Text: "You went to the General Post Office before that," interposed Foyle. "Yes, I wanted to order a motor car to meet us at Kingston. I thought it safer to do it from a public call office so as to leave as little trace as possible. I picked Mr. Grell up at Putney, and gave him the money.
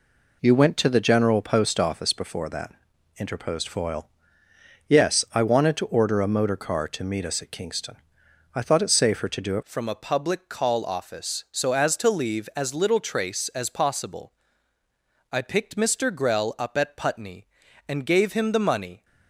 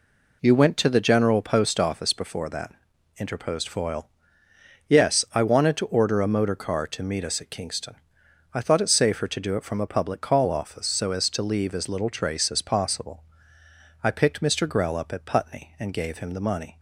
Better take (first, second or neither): second